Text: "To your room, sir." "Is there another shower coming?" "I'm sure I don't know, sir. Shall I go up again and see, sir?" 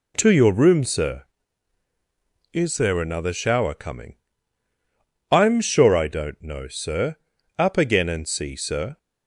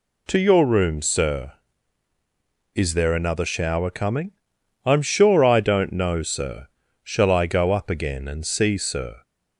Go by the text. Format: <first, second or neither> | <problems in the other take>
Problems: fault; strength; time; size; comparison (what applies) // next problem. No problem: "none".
second | skips "Shall I go"; at 7.3 s